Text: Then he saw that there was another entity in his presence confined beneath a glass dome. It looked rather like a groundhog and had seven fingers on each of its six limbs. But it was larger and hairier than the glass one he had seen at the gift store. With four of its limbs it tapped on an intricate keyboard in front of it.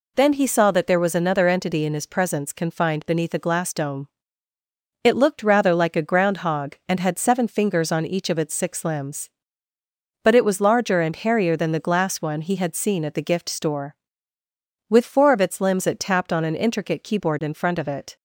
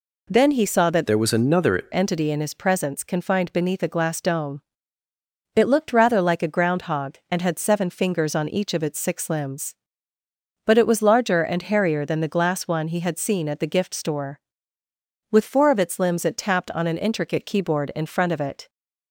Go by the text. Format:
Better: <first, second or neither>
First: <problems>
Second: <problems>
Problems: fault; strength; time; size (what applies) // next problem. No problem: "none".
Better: first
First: none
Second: changes voice from "there" to "another"; from 1.0 to 1.8 s; 0.8 s long